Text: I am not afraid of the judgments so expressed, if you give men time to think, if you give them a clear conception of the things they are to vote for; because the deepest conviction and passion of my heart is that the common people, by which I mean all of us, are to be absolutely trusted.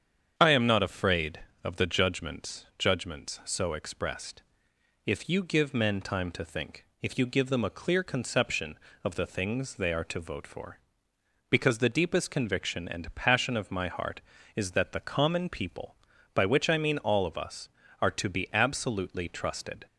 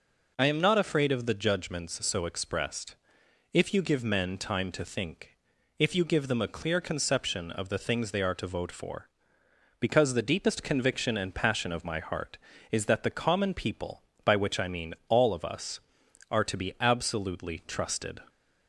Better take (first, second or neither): second